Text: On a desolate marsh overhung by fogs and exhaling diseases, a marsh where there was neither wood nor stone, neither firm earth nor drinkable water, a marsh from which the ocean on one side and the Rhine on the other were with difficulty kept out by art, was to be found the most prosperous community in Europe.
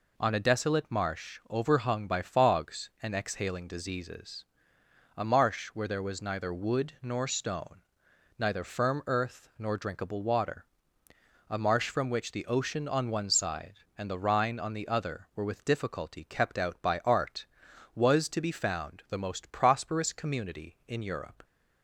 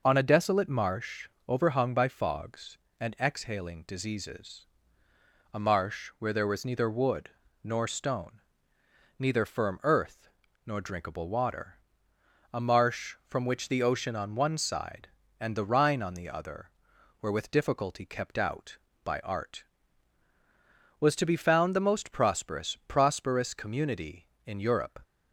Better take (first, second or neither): first